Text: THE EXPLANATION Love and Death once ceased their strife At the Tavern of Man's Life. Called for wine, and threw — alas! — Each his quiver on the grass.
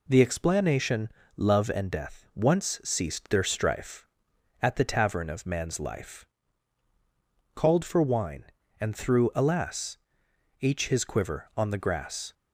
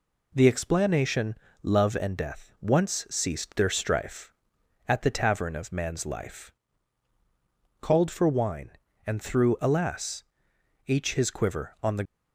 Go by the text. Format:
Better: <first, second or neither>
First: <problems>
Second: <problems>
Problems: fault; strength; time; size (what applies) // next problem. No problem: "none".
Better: first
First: pauses between "EXPLANATION" and "Love"; slight; at 1.1 s; 0.24 s long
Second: pauses between "EXPLANATION" and "Love"; slight; at 1.3 s; 0.24 s long // stops before "grass"; at 12.0 s